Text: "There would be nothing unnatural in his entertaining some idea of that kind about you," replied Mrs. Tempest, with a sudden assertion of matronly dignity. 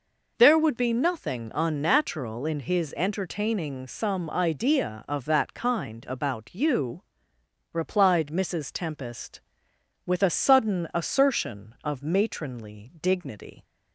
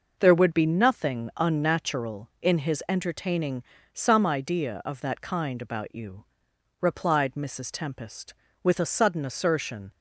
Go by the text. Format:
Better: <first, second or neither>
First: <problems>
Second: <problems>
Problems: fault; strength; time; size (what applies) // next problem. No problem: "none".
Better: first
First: none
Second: pauses between "entertaining" and "some"; slight; at 3.6 s; 0.30 s long // stops before "of matronly dignity"; at 9.9 s